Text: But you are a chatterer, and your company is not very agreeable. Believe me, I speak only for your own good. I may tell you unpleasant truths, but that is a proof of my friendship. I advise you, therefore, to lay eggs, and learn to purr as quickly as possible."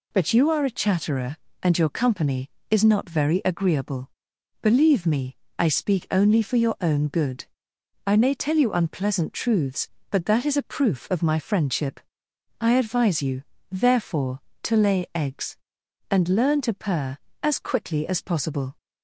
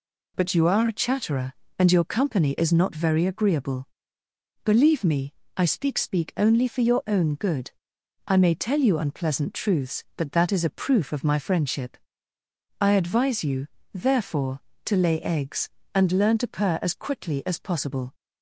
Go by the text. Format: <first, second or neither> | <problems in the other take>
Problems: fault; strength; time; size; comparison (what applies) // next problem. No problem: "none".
first | says "speak" twice; at 5.9 s